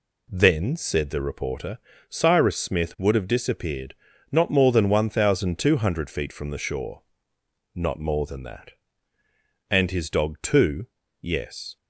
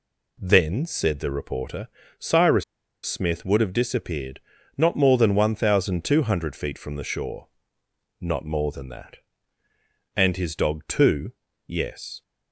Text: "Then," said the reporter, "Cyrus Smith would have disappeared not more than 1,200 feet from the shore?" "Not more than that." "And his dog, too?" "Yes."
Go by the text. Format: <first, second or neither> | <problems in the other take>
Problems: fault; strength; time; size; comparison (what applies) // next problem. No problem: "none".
first | pauses between "Cyrus" and "Smith"; at 2.6 s; 0.41 s long // pauses between "disappeared" and "not"; slight; at 4.3 s; 0.36 s long; slight in the first